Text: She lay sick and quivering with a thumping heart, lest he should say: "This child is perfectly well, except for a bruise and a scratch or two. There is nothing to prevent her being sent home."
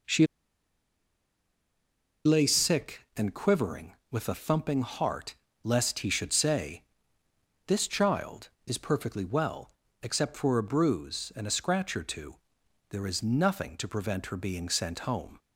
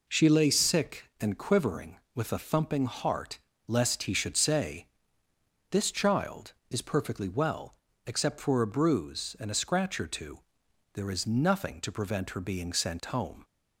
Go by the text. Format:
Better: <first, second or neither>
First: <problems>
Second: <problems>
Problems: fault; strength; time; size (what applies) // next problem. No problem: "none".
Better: second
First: pauses between "She" and "lay"; strong; at 0.2 s; 1.9 s long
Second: none